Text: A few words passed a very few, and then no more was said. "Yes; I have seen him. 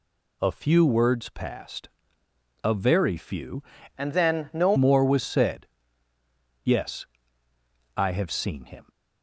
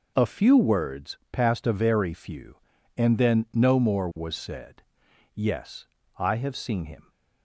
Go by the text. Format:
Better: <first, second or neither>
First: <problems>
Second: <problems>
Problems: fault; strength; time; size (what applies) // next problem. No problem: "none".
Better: second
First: pauses between "passed" and "a"; noticeable; at 1.8 s; 0.74 s long // changes voice from "and" to "no"; from 3.9 to 4.7 s; 0.8 s long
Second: none